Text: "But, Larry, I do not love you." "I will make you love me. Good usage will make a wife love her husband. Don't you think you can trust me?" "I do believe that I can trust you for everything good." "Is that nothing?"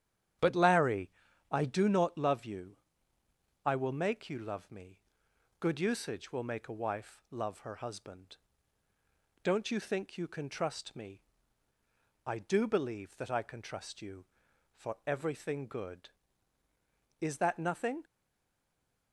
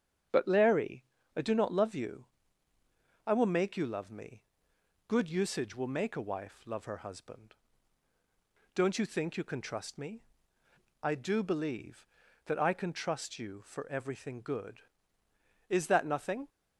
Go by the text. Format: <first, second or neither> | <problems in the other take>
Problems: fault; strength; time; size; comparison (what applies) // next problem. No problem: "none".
second | starts louder than the rest; strong; until 1.8 s; 10 dB; strong in the second // stays silent after the last word; from 18.0 s on; 1.1 s long